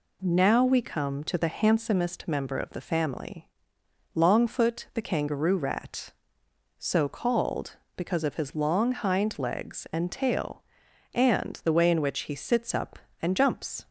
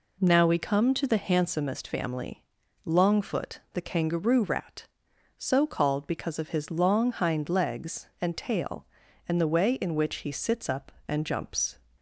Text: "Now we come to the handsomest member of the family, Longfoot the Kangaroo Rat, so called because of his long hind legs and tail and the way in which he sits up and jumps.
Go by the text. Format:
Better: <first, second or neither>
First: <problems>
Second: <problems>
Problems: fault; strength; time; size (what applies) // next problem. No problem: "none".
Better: first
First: none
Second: skips "member of the"; at 1.8 s